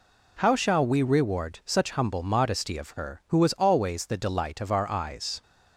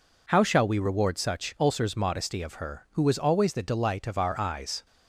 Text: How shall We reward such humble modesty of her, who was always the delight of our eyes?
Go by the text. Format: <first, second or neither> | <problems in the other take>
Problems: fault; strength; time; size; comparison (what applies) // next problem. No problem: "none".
first | says "ulcers" for "humble"; at 1.5 s